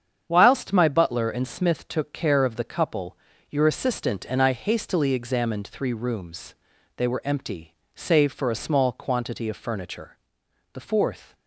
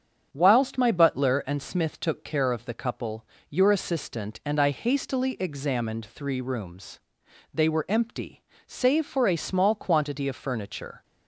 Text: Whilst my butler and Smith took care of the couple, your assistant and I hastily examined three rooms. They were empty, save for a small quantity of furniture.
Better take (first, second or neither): second